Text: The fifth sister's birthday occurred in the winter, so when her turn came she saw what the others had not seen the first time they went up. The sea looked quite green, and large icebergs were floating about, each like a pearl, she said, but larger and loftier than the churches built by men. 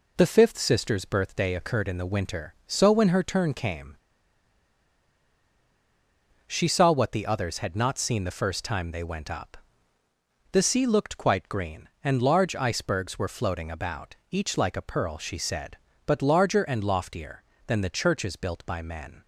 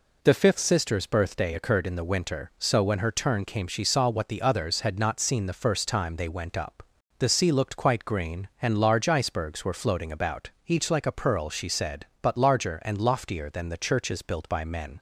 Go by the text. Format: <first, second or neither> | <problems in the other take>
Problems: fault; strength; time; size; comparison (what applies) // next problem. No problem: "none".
second | pauses between "came" and "she"; strong; at 3.9 s; 2.5 s long